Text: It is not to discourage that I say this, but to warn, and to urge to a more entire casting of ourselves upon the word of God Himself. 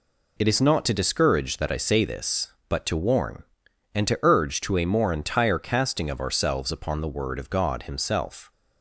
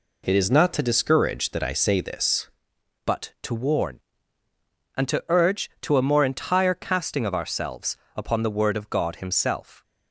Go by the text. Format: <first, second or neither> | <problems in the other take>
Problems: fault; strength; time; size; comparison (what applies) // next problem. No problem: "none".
first | changes voice at "but"; from 3.0 s on; 6.8 s long // pauses between "ourselves" and "upon"; slight; at 7.9 s; 0.18 s long